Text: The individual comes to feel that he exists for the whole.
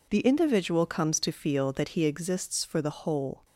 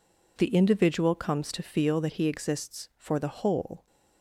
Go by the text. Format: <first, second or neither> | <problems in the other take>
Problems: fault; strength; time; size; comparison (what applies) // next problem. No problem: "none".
neither | none